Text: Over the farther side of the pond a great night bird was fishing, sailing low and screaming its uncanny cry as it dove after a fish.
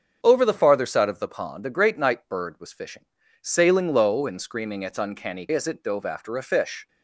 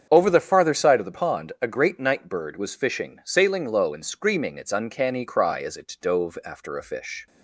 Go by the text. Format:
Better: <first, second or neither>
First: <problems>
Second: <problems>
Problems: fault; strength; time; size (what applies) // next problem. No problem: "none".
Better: second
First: starts louder than the rest; until 1.2 s; 6.5 dB // skips "cry"; at 5.4 s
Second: starts louder than the rest; strong; until 1.1 s; 7.5 dB